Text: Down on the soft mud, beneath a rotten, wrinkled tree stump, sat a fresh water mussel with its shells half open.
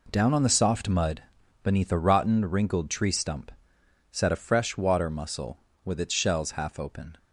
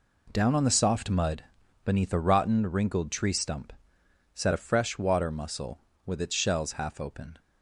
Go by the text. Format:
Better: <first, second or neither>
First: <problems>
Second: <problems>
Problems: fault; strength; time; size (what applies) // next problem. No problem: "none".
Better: neither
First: none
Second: none